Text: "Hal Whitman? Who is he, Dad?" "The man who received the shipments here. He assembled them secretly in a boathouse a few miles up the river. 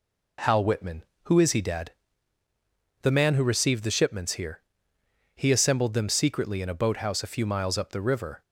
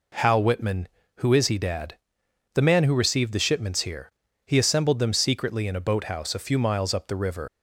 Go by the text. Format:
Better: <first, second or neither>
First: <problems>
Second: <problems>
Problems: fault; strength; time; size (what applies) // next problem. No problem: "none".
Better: first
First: none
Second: leaves "river" unfinished; at 7.4 s; 90 ms